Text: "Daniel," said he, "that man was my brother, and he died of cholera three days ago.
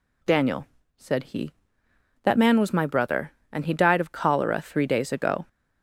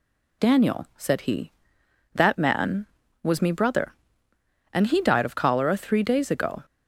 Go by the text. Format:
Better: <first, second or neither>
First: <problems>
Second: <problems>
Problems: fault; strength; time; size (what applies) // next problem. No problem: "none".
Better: first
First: none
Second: says "me" for "my"; at 3.4 s